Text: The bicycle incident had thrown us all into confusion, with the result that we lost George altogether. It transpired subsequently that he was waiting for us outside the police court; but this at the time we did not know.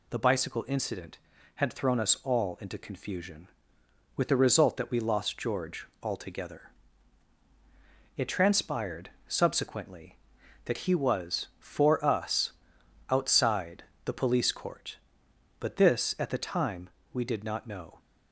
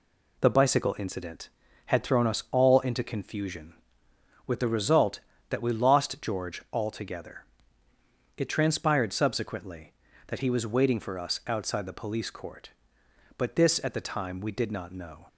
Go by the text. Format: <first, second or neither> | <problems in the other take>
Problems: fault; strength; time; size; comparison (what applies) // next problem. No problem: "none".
second | pauses between "George" and "altogether"; slight; at 5.8 s; 0.16 s long // pauses between "transpired" and "subsequently"; slight; at 9.1 s; 0.16 s long // skips "waiting"; at 11.5 s // pauses between "us" and "outside"; noticeable; at 12.5 s; 0.58 s long // pauses between "outside" and "the"; slight; at 13.8 s; 0.22 s long // pauses between "time" and "we"; slight; at 16.8 s; 0.24 s long